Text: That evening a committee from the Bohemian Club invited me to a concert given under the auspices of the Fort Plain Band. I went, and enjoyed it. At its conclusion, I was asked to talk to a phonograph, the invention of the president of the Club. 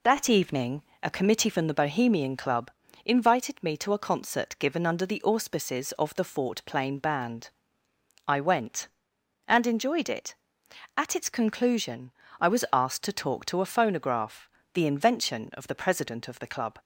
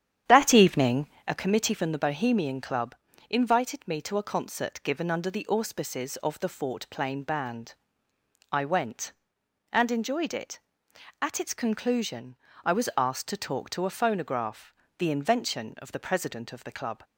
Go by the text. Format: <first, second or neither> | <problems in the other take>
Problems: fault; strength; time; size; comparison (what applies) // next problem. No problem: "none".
first | starts louder than the rest; strong; until 1.4 s; 9.5 dB // pauses between "evening" and "a"; slight; at 1.0 s; 0.22 s long; slight in the first // pauses between "Club" and "invited"; slight; at 2.9 s; 0.34 s long; slight in the first